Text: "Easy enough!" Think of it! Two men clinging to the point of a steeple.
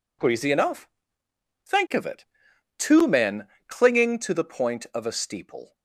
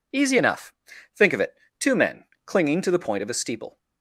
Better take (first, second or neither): second